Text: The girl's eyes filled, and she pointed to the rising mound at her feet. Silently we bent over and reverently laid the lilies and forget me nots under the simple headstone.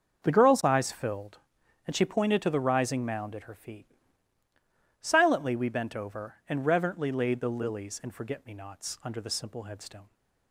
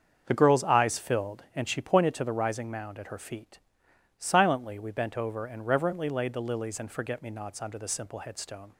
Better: neither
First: starts louder than the rest; until 1.2 s; 6.5 dB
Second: starts louder than the rest; until 1.2 s; 7 dB

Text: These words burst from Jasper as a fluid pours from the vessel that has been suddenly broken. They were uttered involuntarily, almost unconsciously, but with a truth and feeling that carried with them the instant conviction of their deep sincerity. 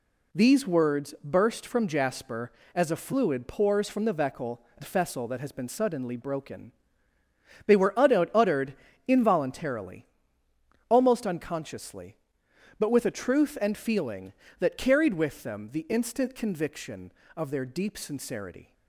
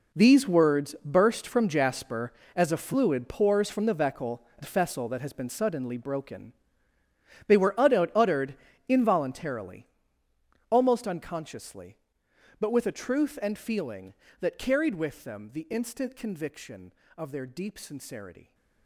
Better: first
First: pauses between "uttered" and "involuntarily"; slight; at 8.7 s; 0.32 s long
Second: gets quieter; strong; throughout; 12.5 dB // pauses between "uttered" and "involuntarily"; slight; at 8.5 s; 0.32 s long

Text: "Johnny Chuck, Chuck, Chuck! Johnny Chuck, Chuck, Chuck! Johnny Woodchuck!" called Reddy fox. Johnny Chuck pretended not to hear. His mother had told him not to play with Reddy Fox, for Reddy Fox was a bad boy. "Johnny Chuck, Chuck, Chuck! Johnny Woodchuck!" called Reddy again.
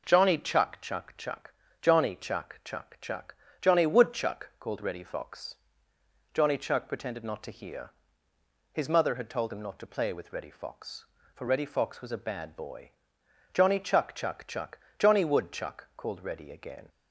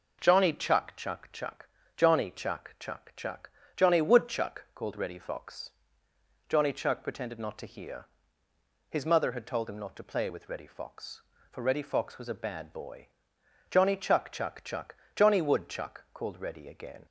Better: neither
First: none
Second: none

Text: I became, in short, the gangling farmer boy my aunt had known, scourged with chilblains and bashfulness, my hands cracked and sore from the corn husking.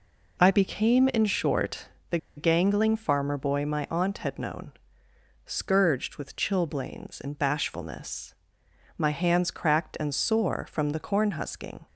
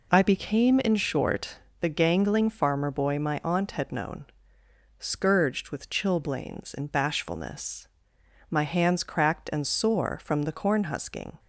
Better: second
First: pauses between "the" and "gangling"; slight; at 2.1 s; 0.19 s long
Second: none

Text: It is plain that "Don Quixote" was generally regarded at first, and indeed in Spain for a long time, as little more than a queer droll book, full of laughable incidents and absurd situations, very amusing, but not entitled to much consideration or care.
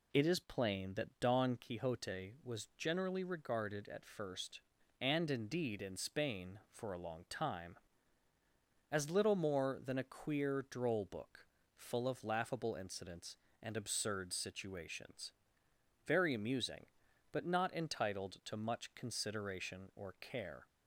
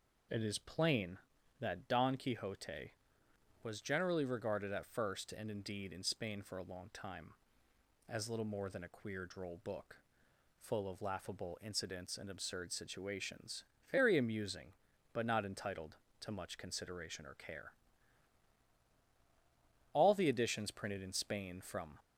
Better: first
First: none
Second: goes on to say "All the editions printed in Spain from"; strong; from 19.9 s on; 2.0 s long

